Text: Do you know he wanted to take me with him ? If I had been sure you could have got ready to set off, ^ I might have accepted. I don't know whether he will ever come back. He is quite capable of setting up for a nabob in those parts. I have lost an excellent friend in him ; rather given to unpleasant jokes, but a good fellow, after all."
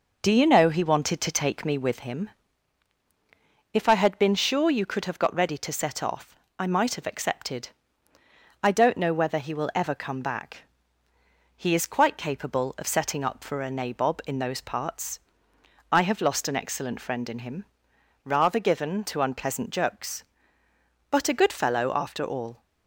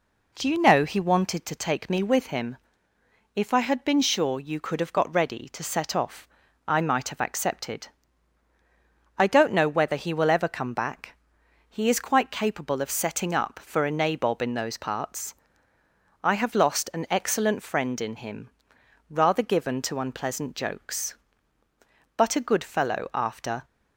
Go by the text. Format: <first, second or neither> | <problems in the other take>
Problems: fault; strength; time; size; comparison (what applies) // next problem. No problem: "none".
first | stops before "all"; at 23.6 s